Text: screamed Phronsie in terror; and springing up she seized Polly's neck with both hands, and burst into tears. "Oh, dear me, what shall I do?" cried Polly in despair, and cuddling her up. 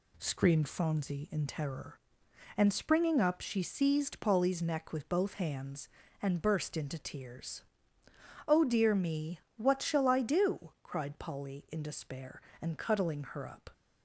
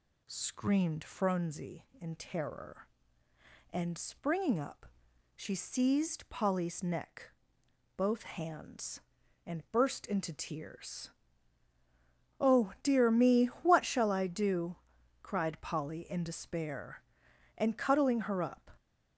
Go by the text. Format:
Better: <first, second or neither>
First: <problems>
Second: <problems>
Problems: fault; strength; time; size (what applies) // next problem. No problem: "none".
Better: first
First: none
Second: pauses between "up" and "she"; noticeable; at 4.8 s; 0.50 s long // skips "with"; at 7.6 s